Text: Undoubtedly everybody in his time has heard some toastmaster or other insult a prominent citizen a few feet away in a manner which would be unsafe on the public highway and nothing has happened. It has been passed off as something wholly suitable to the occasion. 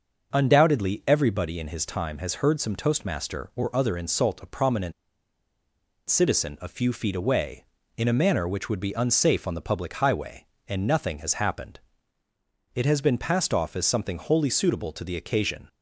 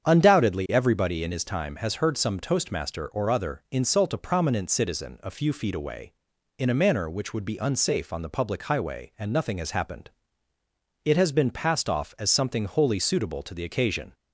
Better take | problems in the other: second | starts louder than the rest; until 1.3 s; 6.5 dB; strong in the second // pauses between "prominent" and "citizen"; at 4.9 s; 1.1 s long

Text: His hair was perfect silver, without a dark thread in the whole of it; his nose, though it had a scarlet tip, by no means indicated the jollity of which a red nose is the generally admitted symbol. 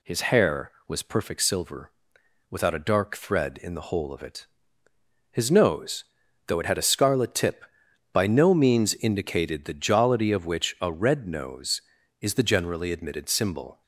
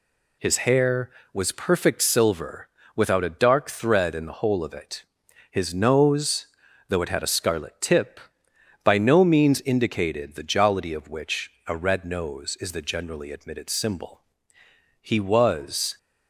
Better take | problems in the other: first | pauses between "which" and "a"; slight; at 11.5 s; 0.16 s long // goes on to say "He was"; noticeable; from 15.0 s on; 0.96 s long

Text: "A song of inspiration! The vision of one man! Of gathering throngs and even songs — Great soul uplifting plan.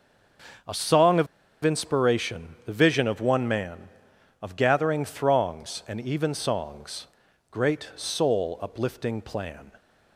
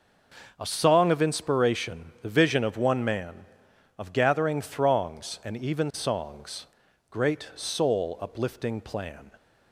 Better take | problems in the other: second | pauses between "of" and "inspiration"; at 1.2 s; 0.37 s long

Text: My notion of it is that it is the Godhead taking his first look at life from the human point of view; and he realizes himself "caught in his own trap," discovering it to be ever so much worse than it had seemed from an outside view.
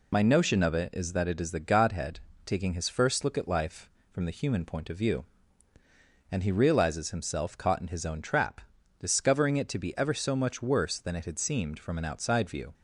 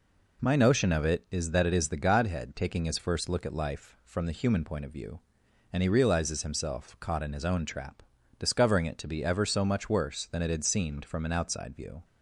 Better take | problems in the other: second | loses the start of "My"; at 0.1 s; 25 ms // pauses between "Godhead" and "taking"; slight; at 2.1 s; 0.24 s long

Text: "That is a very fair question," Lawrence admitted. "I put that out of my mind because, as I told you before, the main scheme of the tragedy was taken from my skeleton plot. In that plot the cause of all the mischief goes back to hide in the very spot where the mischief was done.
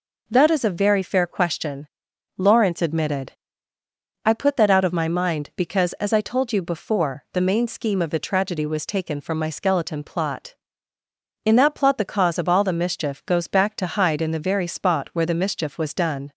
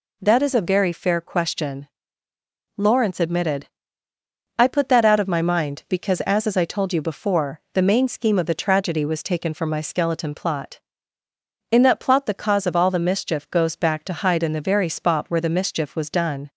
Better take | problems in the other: first | says "as" twice; at 6.4 s

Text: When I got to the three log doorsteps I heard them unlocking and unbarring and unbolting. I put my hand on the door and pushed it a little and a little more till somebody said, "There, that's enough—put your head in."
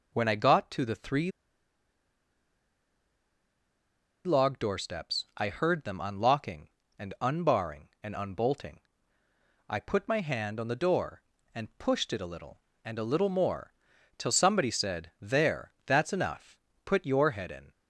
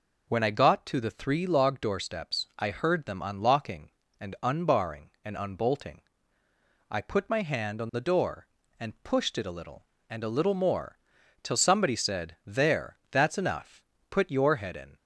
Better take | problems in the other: second | pauses between "three" and "log"; strong; at 1.3 s; 2.9 s long // pauses between "more" and "till"; noticeable; at 13.7 s; 0.46 s long; noticeable in the second

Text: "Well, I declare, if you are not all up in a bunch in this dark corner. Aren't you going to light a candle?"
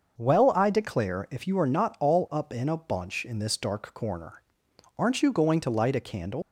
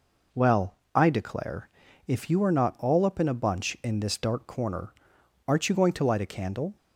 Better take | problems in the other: second | starts louder than the rest; until 1.2 s; 6 dB // leaves "candle" unfinished; at 6.4 s; 90 ms

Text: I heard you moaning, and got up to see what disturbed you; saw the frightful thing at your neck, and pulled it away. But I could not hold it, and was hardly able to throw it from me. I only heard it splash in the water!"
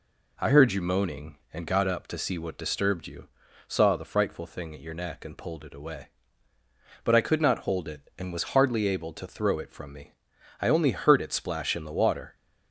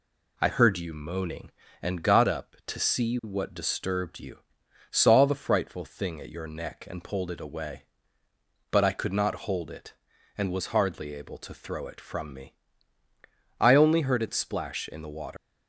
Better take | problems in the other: first | leaves "water" unfinished; at 15.3 s; 140 ms

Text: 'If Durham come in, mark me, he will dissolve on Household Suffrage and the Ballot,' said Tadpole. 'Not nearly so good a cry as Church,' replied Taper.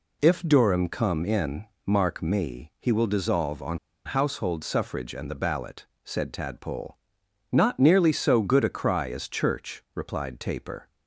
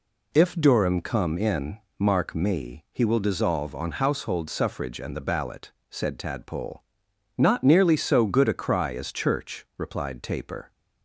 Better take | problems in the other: second | pauses between "on" and "Household"; slight; at 3.7 s; 0.27 s long

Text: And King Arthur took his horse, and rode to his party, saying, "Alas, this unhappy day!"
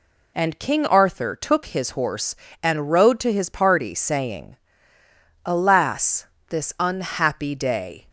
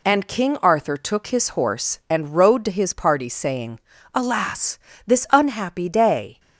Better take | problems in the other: neither | none

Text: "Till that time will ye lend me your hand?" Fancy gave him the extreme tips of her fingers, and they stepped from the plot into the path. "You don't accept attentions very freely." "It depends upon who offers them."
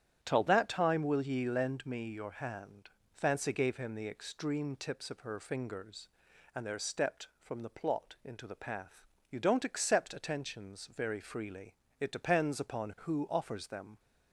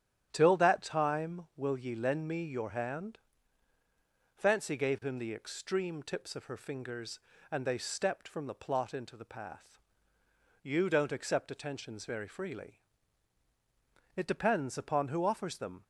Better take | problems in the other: second | starts louder than the rest; strong; until 1.2 s; 10 dB; strong in the second // says "there" for "they"; at 6.6 s

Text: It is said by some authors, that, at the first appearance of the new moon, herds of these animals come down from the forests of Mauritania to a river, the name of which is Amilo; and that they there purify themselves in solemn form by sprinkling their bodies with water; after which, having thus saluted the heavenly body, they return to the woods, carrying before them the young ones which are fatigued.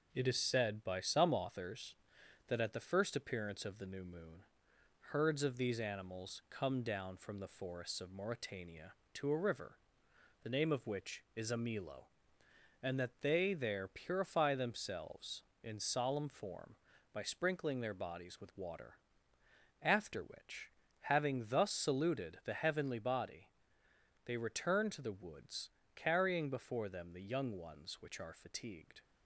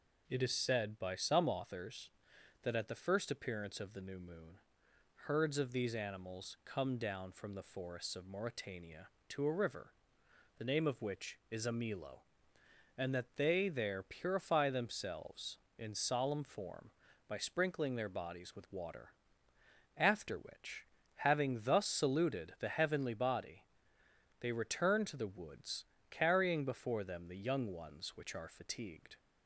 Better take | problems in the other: second | gets quieter; throughout; 3.5 dB

